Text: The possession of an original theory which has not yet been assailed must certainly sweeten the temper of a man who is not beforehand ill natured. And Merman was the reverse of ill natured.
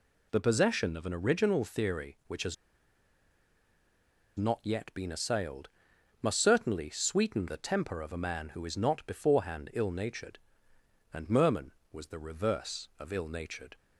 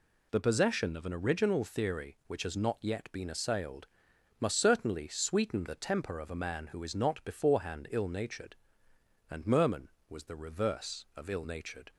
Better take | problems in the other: second | pauses between "has" and "not"; strong; at 2.5 s; 1.8 s long // pauses between "assailed" and "must"; noticeable; at 5.6 s; 0.52 s long; noticeable in the second

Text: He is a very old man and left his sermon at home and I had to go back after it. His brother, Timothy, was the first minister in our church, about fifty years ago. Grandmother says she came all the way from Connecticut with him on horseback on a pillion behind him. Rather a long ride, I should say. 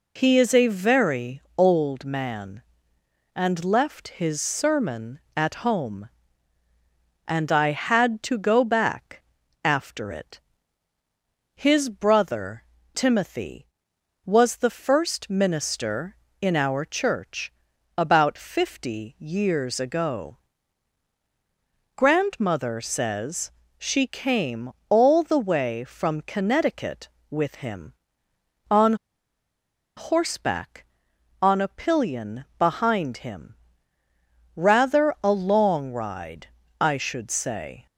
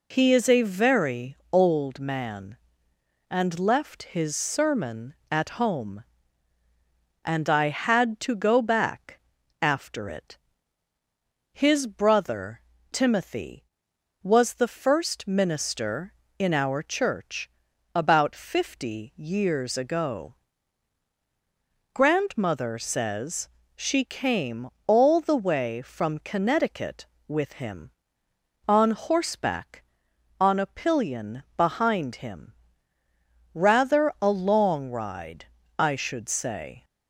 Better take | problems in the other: second | pauses between "very" and "old"; slight; at 1.4 s; 0.16 s long; slight in the second // pauses between "back" and "after"; at 9.2 s; 0.42 s long; also in the second // pauses between "says" and "she"; slight; at 23.5 s; 0.26 s long; slight in the second // pauses between "came" and "all"; slight; at 24.7 s; 0.18 s long; slight in the second // pauses between "on" and "horseback"; at 28.9 s; 1.0 s long

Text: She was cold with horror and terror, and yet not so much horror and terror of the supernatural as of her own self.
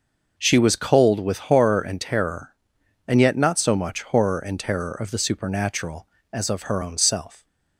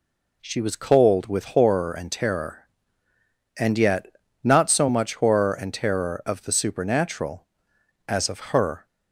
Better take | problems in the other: first | pauses between "yet" and "not"; slight; at 4.1 s; 0.32 s long // stops before "own self"; at 8.8 s

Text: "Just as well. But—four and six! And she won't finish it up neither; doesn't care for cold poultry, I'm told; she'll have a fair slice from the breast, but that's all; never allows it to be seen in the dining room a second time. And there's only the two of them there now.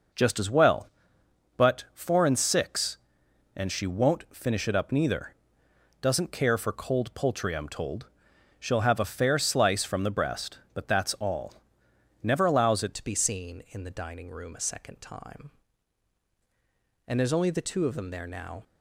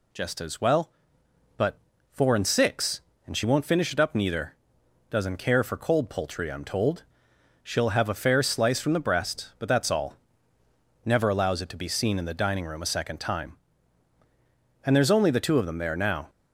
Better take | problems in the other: second | changes voice at "to"; from 12.9 s on; 5.7 s long

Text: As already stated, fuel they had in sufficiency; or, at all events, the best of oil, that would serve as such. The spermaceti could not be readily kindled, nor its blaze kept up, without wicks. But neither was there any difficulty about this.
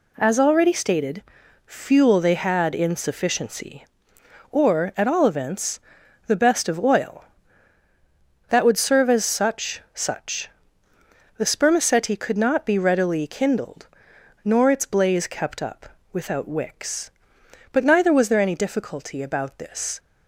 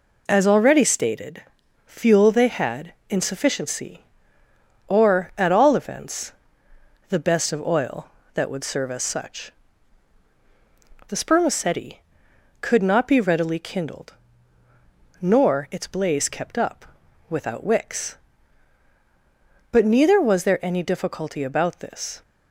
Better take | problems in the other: second | says "such" twice; at 9.9 s

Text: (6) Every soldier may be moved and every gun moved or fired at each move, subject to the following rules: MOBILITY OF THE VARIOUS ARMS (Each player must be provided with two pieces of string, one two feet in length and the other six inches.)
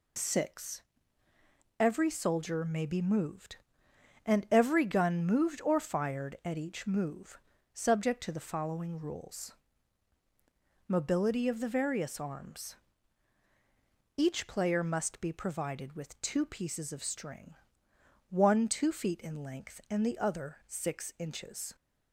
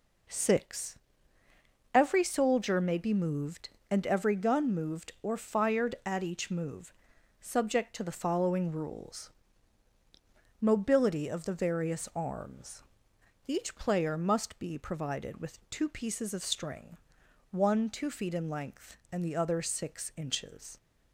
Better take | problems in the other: neither | none

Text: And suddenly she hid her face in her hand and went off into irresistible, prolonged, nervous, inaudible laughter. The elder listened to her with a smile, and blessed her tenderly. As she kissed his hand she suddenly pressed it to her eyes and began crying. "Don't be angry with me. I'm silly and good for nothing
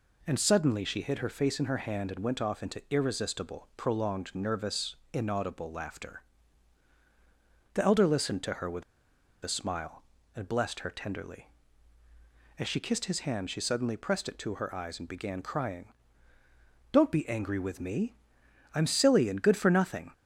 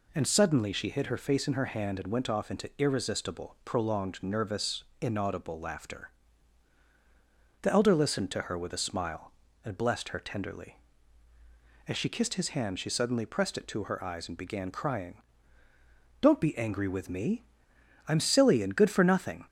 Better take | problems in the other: second | pauses between "with" and "a"; noticeable; at 8.8 s; 0.61 s long

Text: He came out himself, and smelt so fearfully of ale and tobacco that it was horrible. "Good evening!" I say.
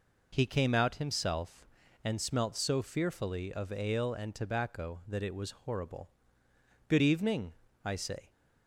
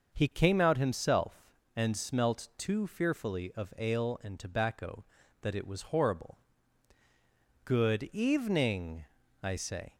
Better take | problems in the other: first | starts louder than the rest; until 1.1 s; 6 dB // says "too" for "so"; at 2.5 s

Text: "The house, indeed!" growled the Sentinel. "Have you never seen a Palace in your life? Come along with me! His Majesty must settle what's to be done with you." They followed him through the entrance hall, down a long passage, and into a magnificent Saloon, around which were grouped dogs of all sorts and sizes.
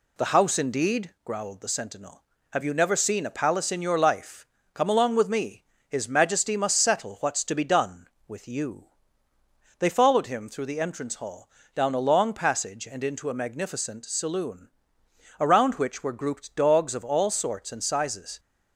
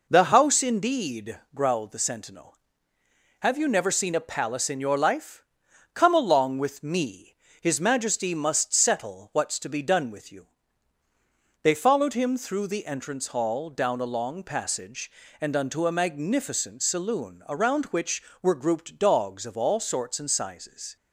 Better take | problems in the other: first | says "unto" for "into"; at 15.5 s

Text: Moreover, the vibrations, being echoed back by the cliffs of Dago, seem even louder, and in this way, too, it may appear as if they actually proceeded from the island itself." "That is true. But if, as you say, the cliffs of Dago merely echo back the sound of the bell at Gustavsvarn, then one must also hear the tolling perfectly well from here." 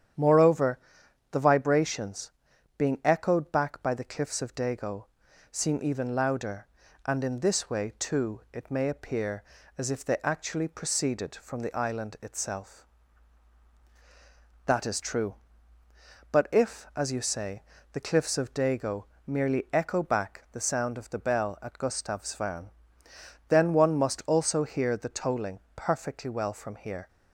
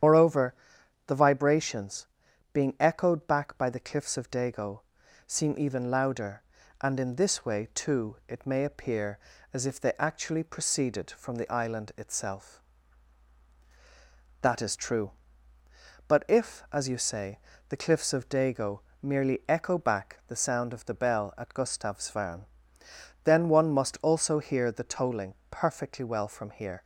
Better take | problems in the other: first | loses the start of "Moreover"; at 0.0 s; 105 ms // starts louder than the rest; strong; until 1.5 s; 9.5 dB; strong in the first // pauses between "Dago" and "merely"; slight; at 18.8 s; 0.20 s long; slight in the first // pauses between "tolling" and "perfectly"; slight; at 25.3 s; 0.16 s long; slight in the first

